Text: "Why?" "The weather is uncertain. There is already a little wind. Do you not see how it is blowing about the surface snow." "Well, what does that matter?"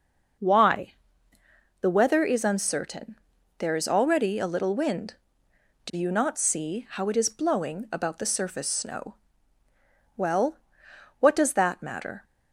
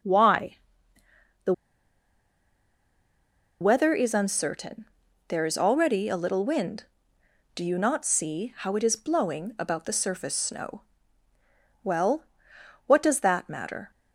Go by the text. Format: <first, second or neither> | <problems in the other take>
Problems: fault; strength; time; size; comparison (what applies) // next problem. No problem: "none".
first | starts louder than the rest; noticeable; until 3.9 s; 6 dB // pauses between "The" and "weather"; strong; at 1.5 s; 2.0 s long